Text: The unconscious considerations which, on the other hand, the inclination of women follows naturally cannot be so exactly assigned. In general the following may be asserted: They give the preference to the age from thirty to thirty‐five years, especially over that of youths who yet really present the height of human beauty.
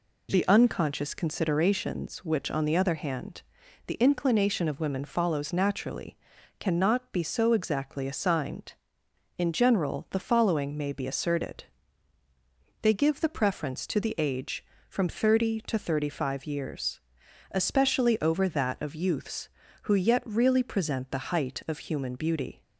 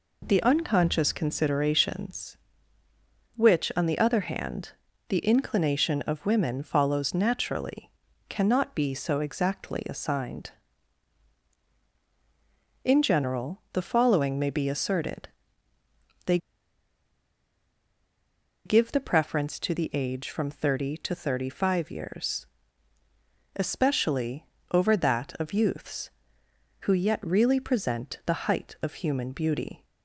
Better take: first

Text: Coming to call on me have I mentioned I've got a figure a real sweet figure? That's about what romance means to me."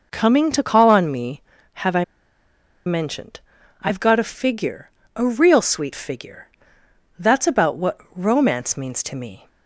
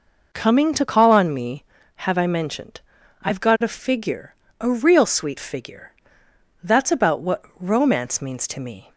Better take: second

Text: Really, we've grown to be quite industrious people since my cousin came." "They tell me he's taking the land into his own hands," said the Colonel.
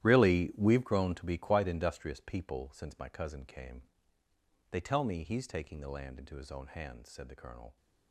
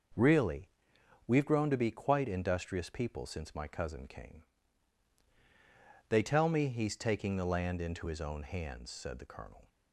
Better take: second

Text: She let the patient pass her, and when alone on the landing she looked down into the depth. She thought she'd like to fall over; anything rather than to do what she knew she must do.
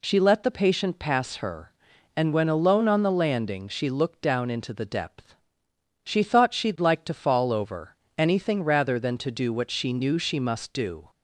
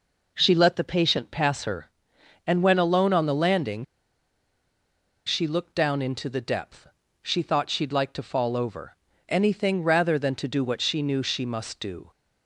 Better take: first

